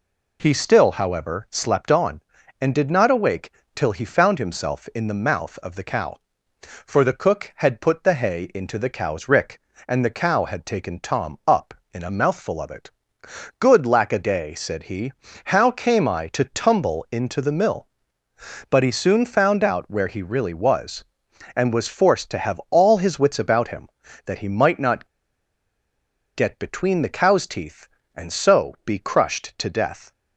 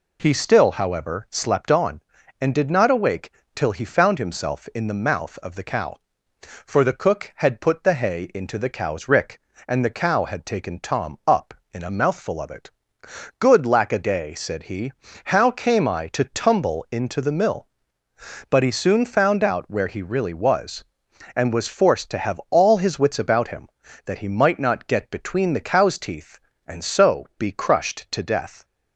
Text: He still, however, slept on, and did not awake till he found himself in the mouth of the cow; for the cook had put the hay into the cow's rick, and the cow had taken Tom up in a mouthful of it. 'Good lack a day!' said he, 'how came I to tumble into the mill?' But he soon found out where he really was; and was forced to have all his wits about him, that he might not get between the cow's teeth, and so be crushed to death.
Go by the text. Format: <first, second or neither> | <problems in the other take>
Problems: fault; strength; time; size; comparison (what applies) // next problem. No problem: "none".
second | pauses between "awake" and "till"; slight; at 3.5 s; 0.24 s long; slight in the second // pauses between "not" and "get"; strong; at 25.0 s; 1.2 s long